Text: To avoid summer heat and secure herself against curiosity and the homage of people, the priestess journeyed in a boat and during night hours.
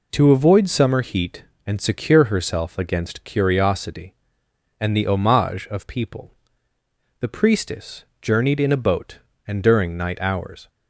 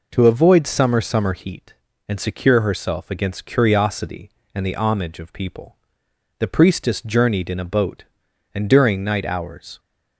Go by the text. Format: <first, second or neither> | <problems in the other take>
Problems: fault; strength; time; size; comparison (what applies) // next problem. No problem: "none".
first | says "summer" twice; at 1.0 s